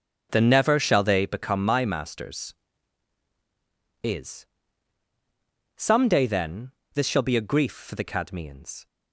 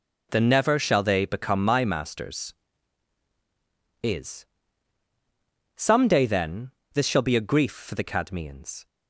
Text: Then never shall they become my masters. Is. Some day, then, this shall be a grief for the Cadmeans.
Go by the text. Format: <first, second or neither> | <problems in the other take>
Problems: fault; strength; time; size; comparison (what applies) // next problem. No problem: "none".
second | starts louder than the rest; until 1.3 s; 7 dB